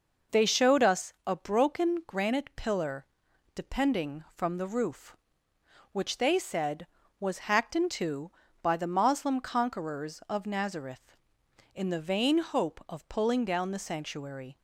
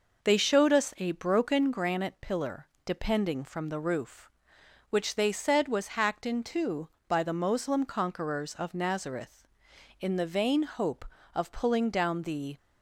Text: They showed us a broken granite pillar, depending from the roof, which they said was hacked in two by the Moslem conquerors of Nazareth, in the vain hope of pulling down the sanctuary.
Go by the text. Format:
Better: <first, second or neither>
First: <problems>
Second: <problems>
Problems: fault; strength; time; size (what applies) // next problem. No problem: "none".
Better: first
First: none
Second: stops before "sanctuary"; at 12.5 s